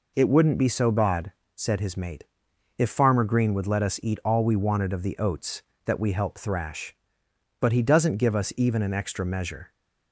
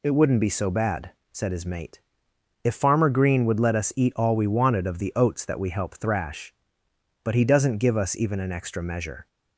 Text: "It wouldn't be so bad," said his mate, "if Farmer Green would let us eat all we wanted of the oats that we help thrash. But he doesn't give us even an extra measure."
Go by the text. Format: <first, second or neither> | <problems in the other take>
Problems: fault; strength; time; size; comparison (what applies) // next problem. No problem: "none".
neither | none